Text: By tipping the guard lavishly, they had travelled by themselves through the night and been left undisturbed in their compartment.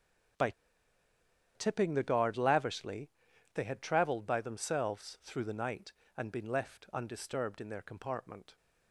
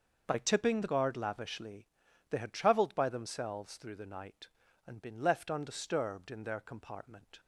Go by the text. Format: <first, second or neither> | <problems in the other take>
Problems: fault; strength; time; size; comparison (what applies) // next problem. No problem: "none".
second | starts louder than the rest; strong; until 2.4 s; 7.5 dB; also in the second // pauses between "By" and "tipping"; at 0.5 s; 1.0 s long